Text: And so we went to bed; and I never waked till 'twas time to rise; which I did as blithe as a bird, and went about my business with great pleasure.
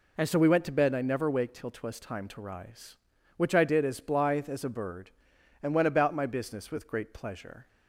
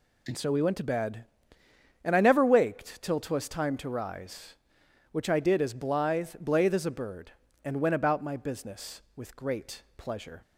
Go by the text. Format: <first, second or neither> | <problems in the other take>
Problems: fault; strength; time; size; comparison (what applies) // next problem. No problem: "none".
first | says "blithe" twice; at 6.4 s